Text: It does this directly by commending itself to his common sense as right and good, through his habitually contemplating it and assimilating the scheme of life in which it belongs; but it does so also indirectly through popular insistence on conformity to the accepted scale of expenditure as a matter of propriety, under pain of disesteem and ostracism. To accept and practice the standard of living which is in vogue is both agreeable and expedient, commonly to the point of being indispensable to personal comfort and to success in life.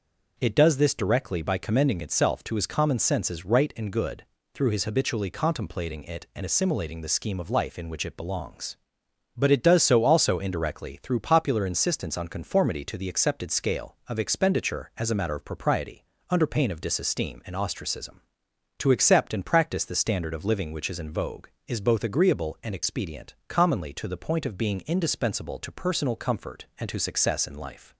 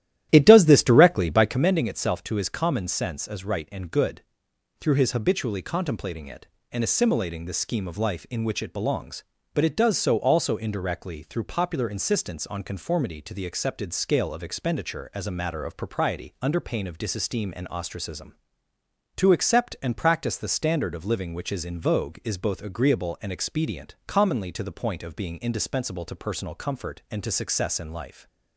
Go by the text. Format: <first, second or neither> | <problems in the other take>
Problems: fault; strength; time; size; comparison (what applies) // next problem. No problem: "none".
first | starts louder than the rest; strong; until 1.7 s; 12.5 dB